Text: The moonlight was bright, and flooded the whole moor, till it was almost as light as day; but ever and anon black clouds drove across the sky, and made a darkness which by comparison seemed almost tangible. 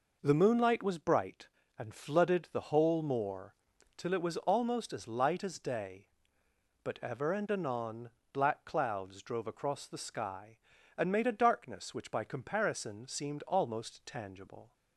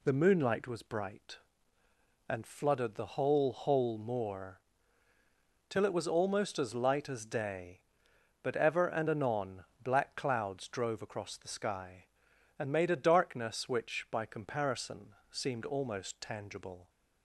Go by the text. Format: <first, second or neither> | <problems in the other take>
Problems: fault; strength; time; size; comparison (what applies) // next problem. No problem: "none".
first | says "whole" twice; at 3.5 s // pauses between "anon" and "black"; slight; at 9.6 s; 0.20 s long; slight in the first // pauses between "comparison" and "seemed"; slight; at 15.1 s; 0.16 s long